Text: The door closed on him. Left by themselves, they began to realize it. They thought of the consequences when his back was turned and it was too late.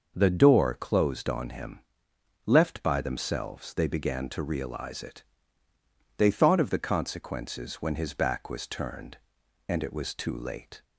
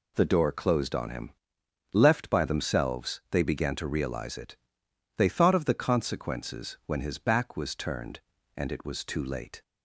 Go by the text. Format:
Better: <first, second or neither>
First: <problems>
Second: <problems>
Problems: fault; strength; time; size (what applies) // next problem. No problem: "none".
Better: neither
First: none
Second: none